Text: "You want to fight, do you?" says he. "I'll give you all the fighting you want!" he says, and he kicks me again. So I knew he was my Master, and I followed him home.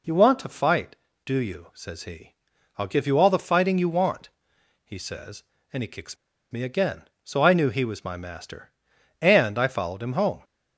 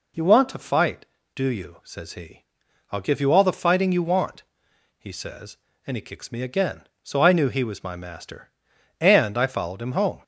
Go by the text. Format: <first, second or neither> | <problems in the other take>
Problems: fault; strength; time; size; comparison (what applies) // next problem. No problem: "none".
second | pauses between "kicks" and "me"; slight; at 6.1 s; 0.35 s long